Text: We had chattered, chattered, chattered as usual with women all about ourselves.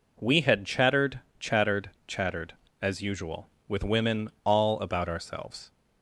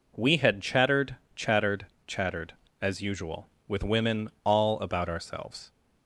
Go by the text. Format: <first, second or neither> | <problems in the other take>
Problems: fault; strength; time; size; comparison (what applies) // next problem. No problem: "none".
neither | none